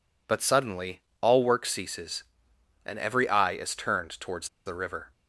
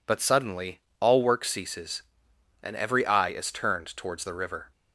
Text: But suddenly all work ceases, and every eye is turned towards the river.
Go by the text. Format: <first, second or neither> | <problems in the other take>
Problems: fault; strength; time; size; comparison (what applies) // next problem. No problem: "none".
second | pauses between "suddenly" and "all"; slight; at 1.0 s; 0.20 s long; slight in the second // pauses between "towards" and "the"; slight; at 4.4 s; 0.19 s long